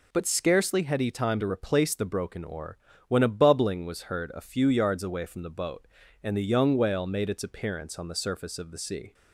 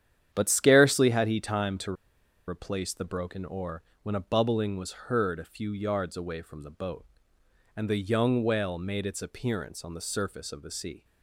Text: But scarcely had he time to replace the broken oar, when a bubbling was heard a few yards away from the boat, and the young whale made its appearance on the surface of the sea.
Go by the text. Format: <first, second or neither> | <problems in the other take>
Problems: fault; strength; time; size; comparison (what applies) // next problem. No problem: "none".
first | starts louder than the rest; strong; until 1.3 s; 9.5 dB // pauses between "to" and "replace"; noticeable; at 1.9 s; 0.53 s long